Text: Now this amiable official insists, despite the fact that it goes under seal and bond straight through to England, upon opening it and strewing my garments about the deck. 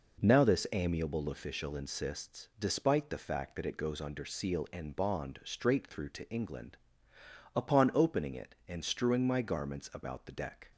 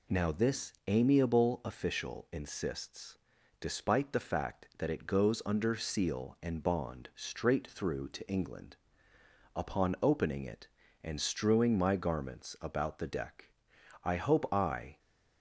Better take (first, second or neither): first